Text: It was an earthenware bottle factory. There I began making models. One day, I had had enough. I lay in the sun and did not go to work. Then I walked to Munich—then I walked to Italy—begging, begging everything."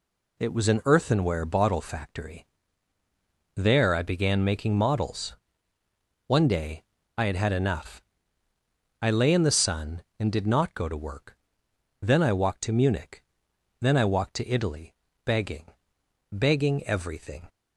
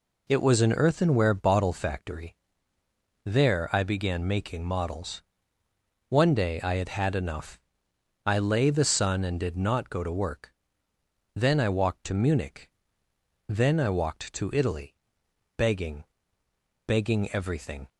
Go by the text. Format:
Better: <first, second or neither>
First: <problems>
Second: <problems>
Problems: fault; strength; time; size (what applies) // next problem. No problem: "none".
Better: first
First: none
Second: skips "in"; at 8.6 s